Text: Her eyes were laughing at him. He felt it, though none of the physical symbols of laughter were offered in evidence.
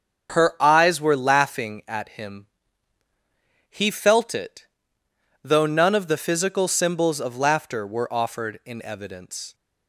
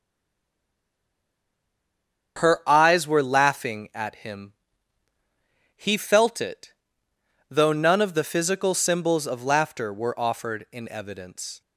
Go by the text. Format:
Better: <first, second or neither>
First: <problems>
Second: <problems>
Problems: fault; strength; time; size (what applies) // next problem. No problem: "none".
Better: first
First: starts louder than the rest; strong; until 1.3 s; 7 dB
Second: stays silent before the first word; until 2.3 s; 2.3 s long // starts louder than the rest; strong; until 3.4 s; 7 dB